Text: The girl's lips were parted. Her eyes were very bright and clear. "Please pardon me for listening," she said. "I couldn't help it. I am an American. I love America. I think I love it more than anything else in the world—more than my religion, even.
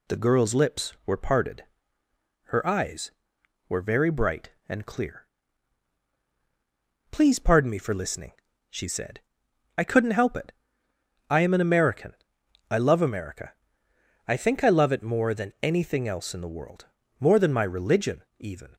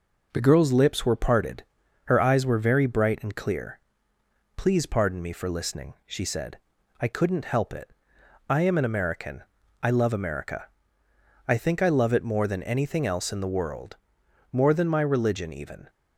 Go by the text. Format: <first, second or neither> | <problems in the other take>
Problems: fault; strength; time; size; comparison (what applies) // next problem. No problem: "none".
neither | none